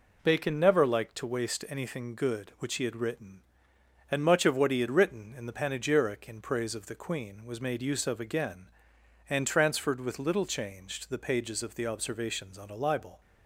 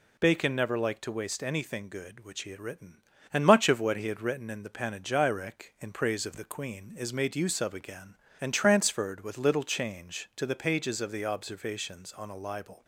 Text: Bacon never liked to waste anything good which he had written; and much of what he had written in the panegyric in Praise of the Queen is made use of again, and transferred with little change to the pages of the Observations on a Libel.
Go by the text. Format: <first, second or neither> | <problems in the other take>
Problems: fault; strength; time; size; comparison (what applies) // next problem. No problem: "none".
second | says "was" for "is"; at 7.4 s